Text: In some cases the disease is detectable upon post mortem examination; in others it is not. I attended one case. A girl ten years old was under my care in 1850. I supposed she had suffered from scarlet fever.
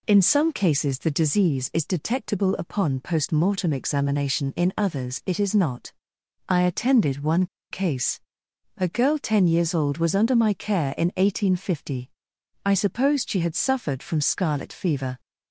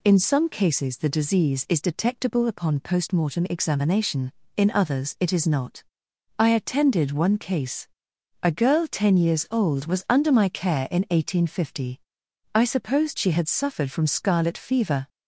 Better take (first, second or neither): second